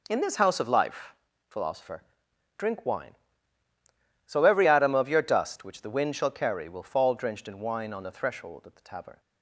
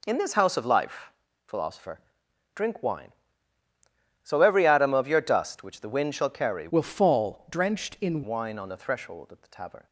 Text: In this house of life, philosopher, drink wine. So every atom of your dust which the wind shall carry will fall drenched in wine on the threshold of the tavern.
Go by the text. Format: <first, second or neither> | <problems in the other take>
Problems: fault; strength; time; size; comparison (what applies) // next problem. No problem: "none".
first | changes voice from "will" to "in"; from 6.6 to 8.2 s; 1.6 s long